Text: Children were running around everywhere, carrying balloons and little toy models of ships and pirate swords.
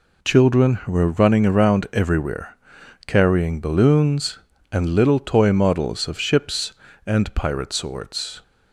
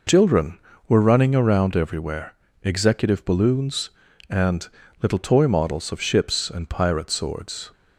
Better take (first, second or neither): first